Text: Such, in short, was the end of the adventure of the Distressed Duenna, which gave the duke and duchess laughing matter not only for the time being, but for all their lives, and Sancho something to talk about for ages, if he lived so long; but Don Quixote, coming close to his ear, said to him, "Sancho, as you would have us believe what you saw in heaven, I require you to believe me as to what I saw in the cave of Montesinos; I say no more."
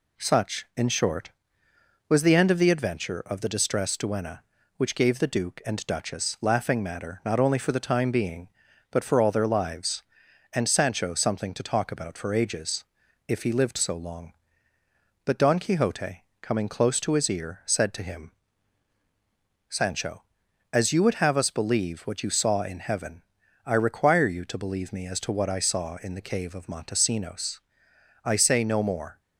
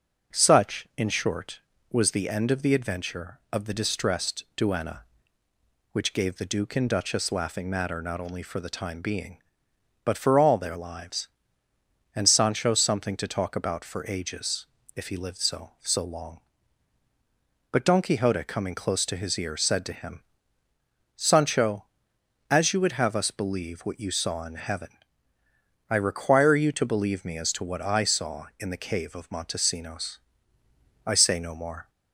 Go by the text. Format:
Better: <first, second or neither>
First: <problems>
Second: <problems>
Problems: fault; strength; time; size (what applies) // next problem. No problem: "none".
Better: first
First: none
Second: says "so" twice; at 15.7 s